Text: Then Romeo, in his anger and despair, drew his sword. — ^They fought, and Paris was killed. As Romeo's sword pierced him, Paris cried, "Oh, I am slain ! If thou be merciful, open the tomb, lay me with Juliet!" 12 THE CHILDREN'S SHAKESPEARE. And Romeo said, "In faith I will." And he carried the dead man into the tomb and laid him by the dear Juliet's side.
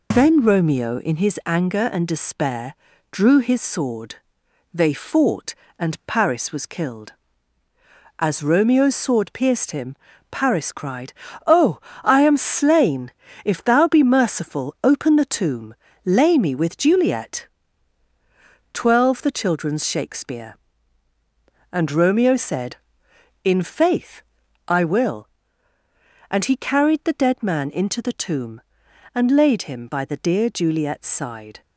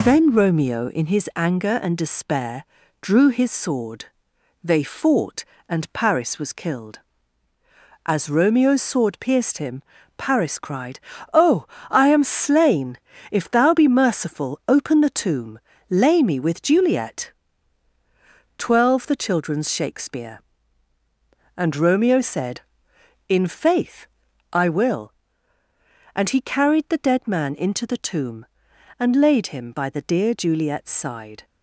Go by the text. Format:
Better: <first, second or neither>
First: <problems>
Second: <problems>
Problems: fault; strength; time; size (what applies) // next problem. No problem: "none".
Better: neither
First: pauses between "faith" and "I"; noticeable; at 24.2 s; 0.46 s long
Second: pauses between "faith" and "I"; noticeable; at 24.0 s; 0.46 s long